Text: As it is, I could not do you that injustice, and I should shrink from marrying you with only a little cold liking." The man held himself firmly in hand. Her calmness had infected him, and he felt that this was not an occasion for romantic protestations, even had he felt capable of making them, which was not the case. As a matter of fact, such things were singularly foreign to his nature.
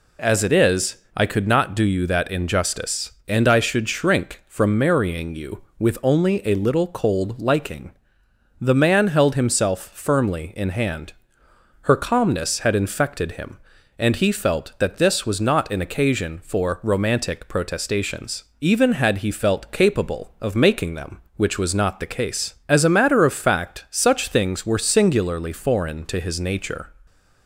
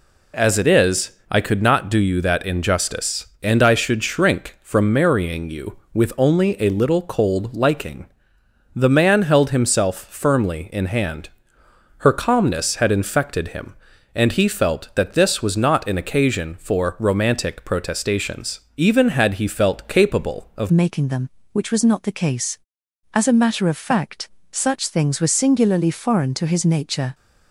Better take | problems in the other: first | changes voice at "making"; from 20.7 s on; 6.4 s long

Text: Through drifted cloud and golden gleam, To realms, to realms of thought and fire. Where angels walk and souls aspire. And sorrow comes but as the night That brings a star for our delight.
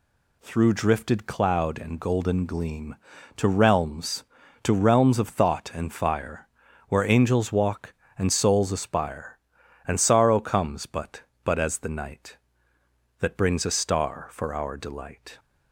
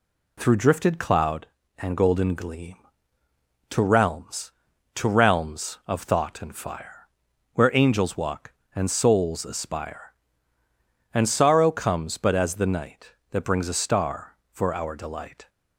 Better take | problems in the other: second | says "but" twice; at 11.4 s

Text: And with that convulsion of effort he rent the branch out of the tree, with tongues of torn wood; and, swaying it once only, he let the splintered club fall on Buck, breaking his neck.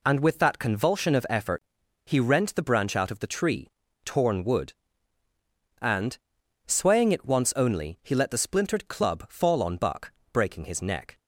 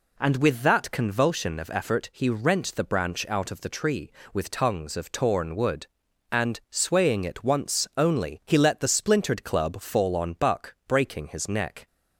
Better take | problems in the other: second | pauses between "effort" and "he"; at 1.6 s; 0.42 s long // skips "with tongues of"; at 3.8 s

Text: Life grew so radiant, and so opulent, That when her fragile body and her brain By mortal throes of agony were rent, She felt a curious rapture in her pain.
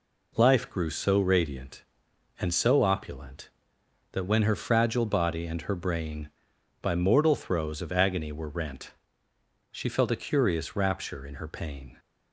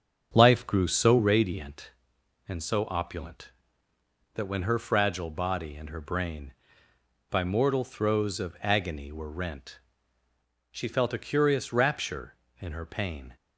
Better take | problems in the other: first | starts louder than the rest; strong; until 1.4 s; 7.5 dB

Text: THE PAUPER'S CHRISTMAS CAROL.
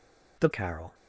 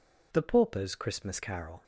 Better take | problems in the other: second | skips "PAUPER'S CHRISTMAS"; at 0.5 s

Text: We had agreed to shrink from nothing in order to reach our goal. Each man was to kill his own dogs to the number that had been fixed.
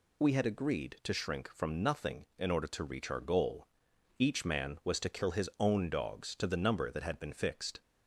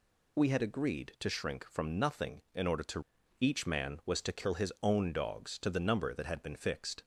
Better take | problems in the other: first | skips "reach our goal"; at 3.1 s

